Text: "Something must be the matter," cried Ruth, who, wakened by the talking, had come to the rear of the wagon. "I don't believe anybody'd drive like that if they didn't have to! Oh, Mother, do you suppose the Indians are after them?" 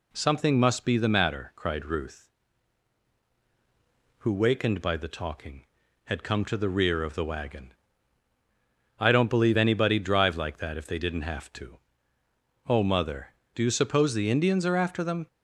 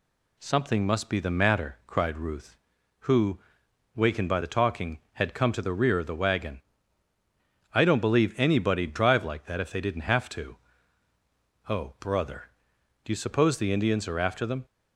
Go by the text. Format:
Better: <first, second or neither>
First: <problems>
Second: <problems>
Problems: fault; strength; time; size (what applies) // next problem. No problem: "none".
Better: first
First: none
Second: says "Brother" for "Mother"; at 12.0 s